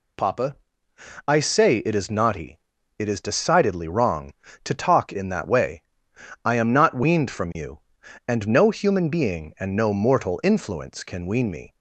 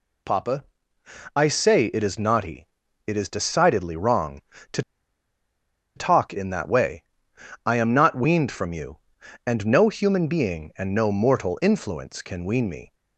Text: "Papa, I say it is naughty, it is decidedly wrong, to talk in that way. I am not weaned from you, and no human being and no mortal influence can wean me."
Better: first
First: none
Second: pauses between "to" and "talk"; at 4.8 s; 1.1 s long

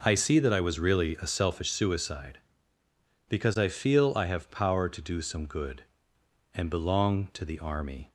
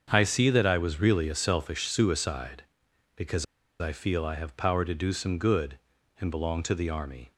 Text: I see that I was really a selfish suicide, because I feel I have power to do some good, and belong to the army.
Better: first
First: none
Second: starts louder than the rest; until 1.1 s; 7 dB // pauses between "because" and "I"; slight; at 3.4 s; 0.35 s long

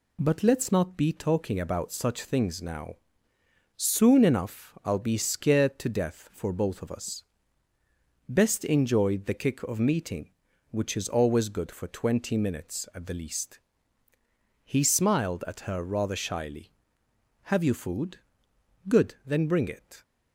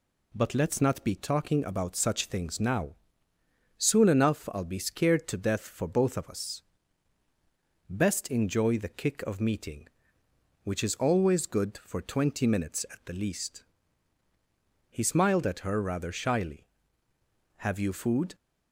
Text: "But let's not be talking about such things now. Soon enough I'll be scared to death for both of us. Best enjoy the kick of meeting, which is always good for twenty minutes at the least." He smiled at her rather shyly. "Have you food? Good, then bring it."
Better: first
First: none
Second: stops before "Good then bring it"; at 18.3 s

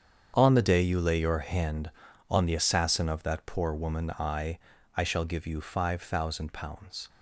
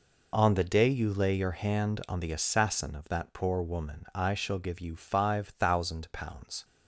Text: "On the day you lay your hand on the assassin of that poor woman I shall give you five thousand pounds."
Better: second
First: starts louder than the rest; strong; until 1.3 s; 7.5 dB // says "I" twice; at 4.9 s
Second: none

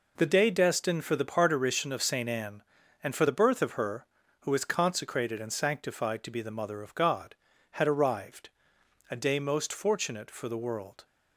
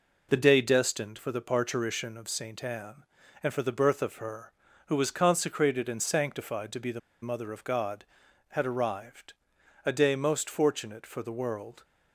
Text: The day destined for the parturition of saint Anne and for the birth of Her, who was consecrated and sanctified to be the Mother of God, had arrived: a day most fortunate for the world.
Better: first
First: none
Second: pauses between "the" and "Mother"; slight; at 6.9 s; 0.22 s long

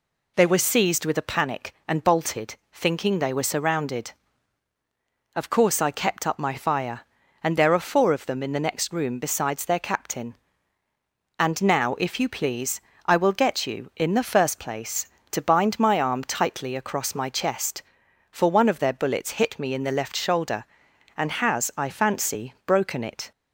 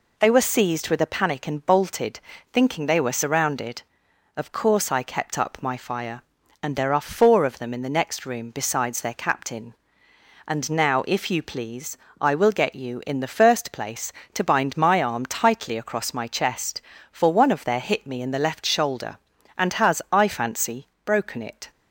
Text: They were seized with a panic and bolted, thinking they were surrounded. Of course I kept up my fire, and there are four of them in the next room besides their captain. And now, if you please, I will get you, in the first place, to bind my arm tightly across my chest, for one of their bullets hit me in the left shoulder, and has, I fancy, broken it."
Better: first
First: none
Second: skips "bullets"; at 17.8 s

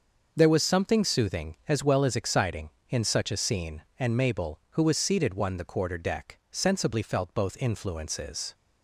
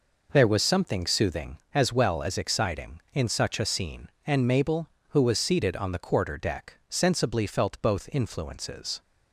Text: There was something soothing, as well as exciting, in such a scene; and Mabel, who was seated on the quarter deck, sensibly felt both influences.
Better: second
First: starts louder than the rest; noticeable; until 1.3 s; 6 dB // says "one" for "on"; at 5.3 s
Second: none

